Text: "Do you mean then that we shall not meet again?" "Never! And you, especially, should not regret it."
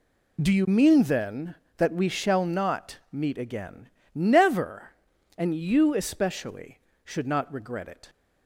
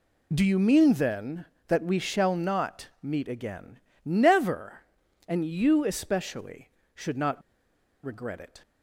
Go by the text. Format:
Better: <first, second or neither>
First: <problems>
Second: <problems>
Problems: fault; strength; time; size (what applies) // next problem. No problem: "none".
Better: first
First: none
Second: pauses between "not" and "regret"; noticeable; at 7.4 s; 0.64 s long